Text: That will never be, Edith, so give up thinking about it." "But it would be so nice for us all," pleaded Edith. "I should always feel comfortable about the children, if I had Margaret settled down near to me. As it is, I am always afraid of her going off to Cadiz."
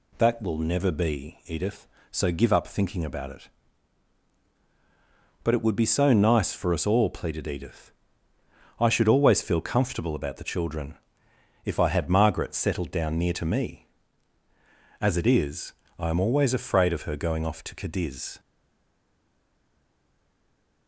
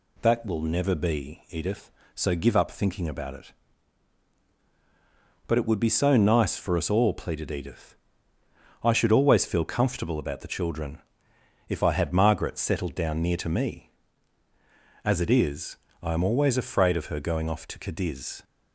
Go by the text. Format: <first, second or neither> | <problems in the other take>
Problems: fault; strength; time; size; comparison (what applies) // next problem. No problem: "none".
second | stays silent after the last word; from 18.3 s on; 2.5 s long